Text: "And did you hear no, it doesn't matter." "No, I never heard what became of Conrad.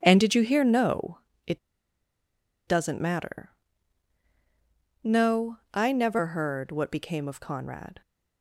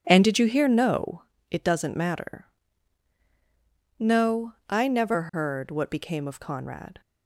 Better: second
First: pauses between "it" and "doesn't"; at 1.5 s; 1.0 s long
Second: none

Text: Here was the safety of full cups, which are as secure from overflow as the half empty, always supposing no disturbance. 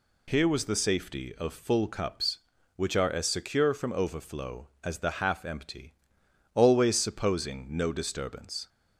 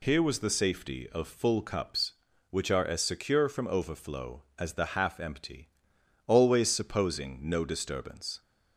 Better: neither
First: none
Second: none

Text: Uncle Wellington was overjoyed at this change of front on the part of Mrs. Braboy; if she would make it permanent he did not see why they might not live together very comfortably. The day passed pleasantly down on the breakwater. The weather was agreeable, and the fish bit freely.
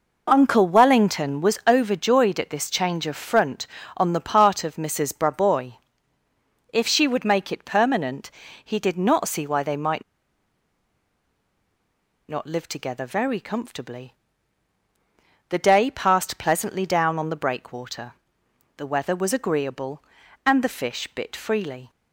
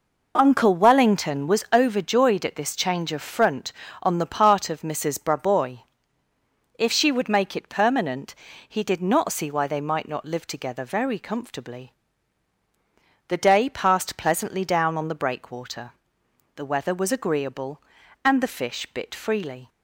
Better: second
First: pauses between "permanent" and "he"; slight; at 8.2 s; 0.34 s long // pauses between "might" and "not"; strong; at 10.0 s; 2.2 s long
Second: pauses between "permanent" and "he"; slight; at 8.3 s; 0.34 s long

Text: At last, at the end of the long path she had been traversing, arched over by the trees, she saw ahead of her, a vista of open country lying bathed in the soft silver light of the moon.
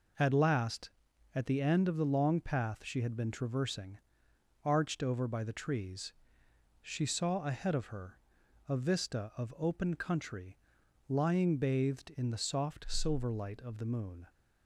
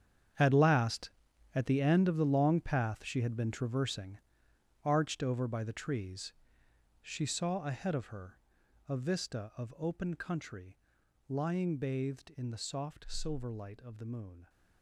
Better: first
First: pauses between "country" and "lying"; noticeable; at 10.5 s; 0.52 s long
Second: gets quieter; strong; throughout; 14.5 dB // pauses between "country" and "lying"; noticeable; at 10.7 s; 0.52 s long

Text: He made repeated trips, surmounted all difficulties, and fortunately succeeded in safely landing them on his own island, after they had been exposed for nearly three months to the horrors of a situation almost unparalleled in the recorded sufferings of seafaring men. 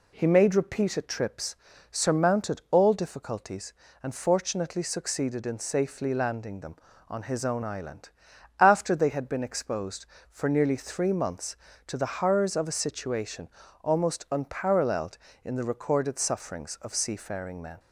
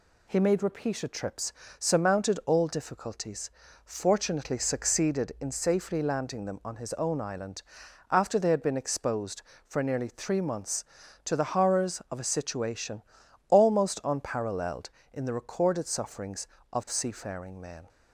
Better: first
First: pauses between "situation" and "almost"; slight; at 13.4 s; 0.36 s long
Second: skips "and"; at 3.6 s // pauses between "situation" and "almost"; noticeable; at 13.0 s; 0.48 s long

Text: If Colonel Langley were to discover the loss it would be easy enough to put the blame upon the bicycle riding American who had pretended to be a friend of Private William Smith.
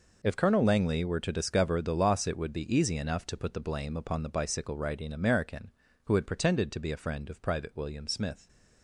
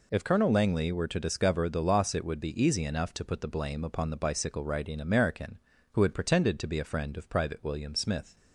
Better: second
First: gets quieter; strong; throughout; 13 dB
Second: none

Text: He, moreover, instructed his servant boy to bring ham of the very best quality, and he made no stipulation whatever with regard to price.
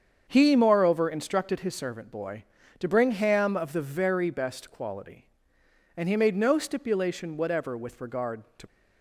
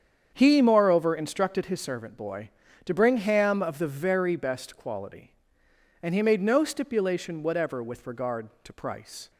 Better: second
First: starts louder than the rest; strong; until 1.2 s; 7.5 dB // stops before "price"; at 8.6 s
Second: starts louder than the rest; strong; until 1.3 s; 8 dB

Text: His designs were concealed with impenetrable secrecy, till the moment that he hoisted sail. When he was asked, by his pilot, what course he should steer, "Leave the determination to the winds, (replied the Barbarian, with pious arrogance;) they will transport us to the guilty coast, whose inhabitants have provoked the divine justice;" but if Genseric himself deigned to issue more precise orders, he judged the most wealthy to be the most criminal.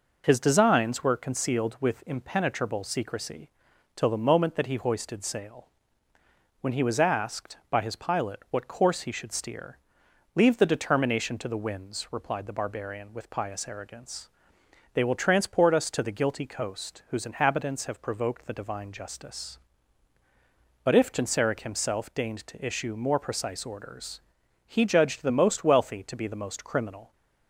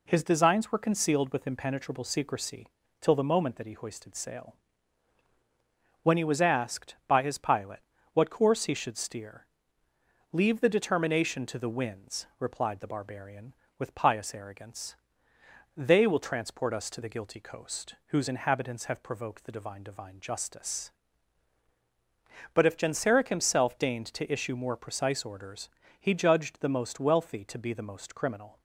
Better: first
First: none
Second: says "divine" twice; at 19.8 s

